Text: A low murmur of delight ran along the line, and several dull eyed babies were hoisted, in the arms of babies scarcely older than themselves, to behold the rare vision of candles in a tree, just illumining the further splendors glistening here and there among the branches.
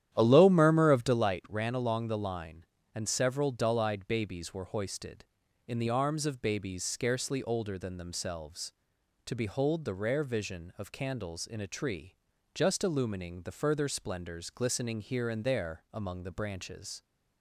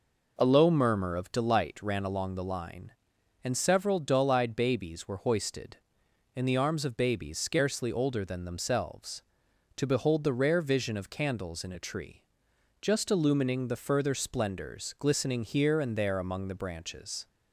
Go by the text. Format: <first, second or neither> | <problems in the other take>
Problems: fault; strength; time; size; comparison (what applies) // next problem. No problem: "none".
second | starts louder than the rest; strong; until 1.3 s; 11 dB